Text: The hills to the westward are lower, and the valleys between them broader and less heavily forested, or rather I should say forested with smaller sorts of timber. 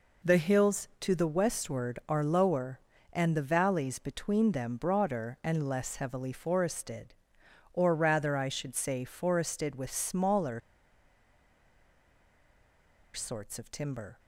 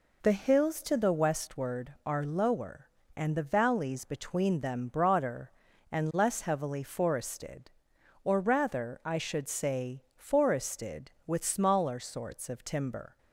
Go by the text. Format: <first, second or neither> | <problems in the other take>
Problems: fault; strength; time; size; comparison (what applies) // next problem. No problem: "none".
second | pauses between "smaller" and "sorts"; strong; at 10.6 s; 2.5 s long